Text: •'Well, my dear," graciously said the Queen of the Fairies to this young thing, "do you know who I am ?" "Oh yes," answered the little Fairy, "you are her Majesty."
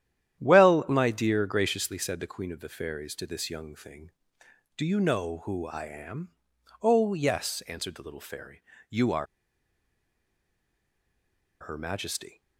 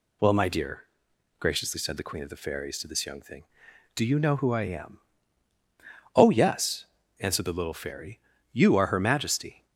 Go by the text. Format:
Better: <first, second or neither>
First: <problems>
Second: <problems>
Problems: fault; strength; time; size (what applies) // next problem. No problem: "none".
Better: second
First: starts louder than the rest; strong; until 1.4 s; 11 dB // pauses between "are" and "her"; strong; at 9.2 s; 2.3 s long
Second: none